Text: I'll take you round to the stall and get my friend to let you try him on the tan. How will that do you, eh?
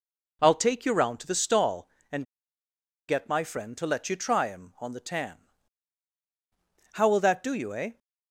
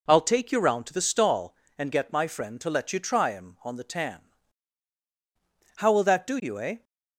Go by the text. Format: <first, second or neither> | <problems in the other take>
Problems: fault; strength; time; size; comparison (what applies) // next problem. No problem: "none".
second | pauses between "and" and "get"; noticeable; at 2.2 s; 0.83 s long